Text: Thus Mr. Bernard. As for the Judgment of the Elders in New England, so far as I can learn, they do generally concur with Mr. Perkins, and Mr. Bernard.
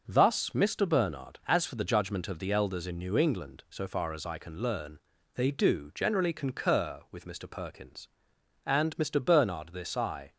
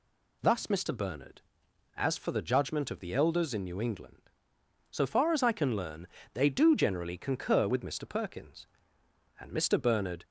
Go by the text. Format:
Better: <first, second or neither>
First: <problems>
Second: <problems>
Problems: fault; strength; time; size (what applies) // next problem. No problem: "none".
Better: second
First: starts louder than the rest; until 1.0 s; 6 dB // goes on to say "This I"; from 9.7 s on; 0.60 s long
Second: none